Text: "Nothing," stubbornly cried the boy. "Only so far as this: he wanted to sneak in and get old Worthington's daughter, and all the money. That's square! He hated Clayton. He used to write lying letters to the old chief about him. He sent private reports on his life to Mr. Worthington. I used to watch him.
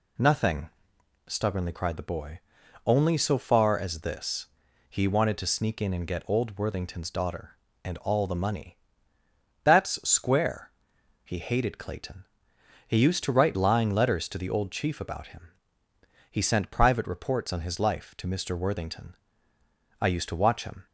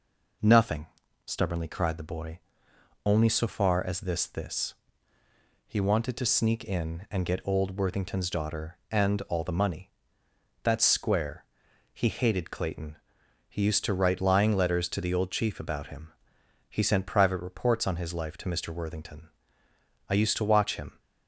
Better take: first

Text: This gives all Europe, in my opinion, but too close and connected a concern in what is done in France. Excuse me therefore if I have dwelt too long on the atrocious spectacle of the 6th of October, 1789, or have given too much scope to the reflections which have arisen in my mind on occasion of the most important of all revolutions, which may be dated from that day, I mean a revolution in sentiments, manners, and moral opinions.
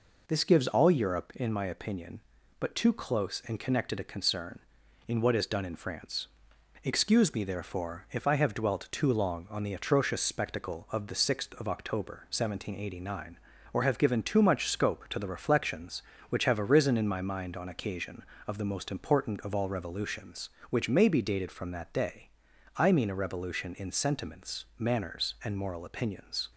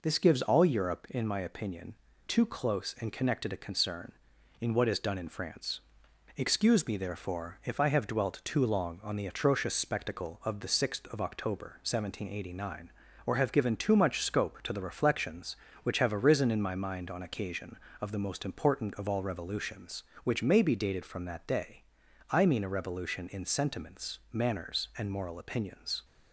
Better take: first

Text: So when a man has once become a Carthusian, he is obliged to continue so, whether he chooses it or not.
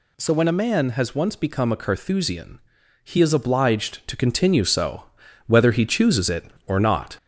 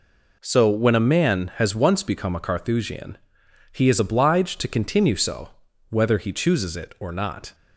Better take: second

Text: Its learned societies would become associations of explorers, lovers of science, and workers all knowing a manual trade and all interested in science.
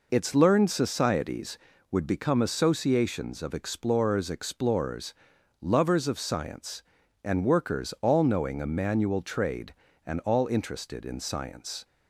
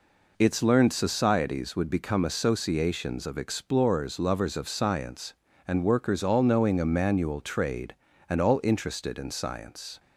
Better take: second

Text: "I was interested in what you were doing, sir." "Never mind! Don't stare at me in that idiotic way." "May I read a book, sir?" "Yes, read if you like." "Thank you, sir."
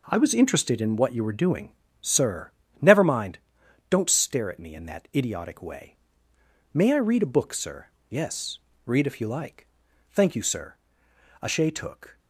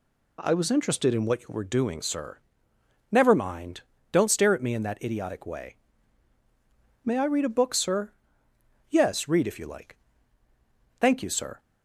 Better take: second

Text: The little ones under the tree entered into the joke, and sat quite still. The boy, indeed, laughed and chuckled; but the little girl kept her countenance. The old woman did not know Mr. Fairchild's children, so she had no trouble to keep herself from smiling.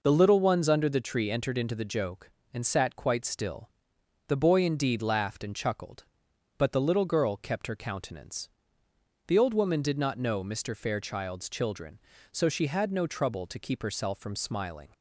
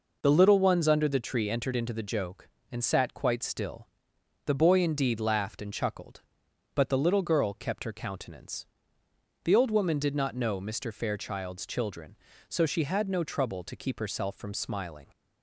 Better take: neither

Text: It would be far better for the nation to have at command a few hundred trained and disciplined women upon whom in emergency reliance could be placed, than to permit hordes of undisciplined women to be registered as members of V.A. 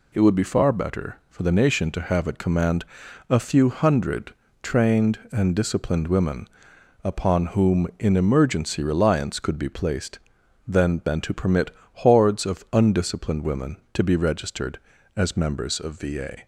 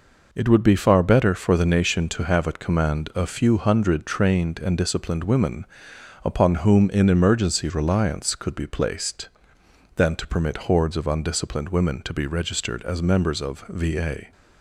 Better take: second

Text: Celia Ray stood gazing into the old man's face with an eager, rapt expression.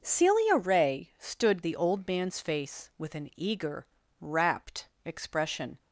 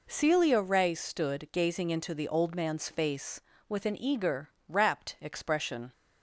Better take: second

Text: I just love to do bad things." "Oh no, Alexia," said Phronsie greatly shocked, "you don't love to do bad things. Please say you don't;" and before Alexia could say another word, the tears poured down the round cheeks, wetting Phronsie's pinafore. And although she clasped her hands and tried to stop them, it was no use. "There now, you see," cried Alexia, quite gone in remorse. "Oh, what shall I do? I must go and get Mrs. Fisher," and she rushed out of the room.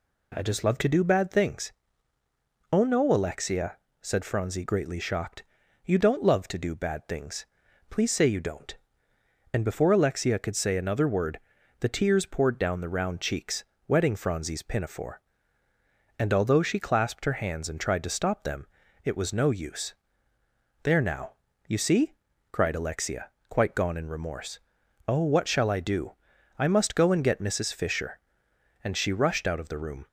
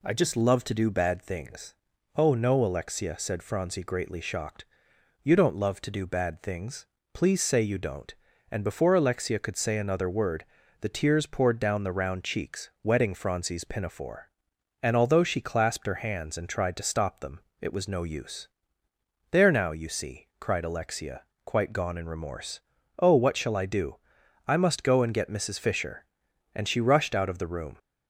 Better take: neither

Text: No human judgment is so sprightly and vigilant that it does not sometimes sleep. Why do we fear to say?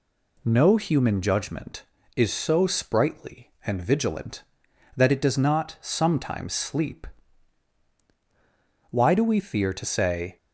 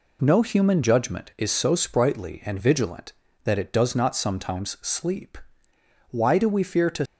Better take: first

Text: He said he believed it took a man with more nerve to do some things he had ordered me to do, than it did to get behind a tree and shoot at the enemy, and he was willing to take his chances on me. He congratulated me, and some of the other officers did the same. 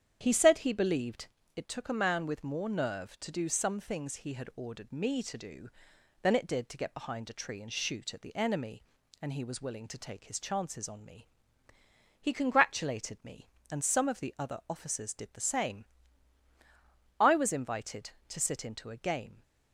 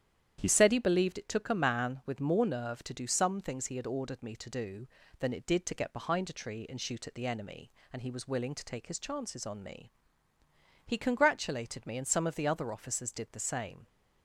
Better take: second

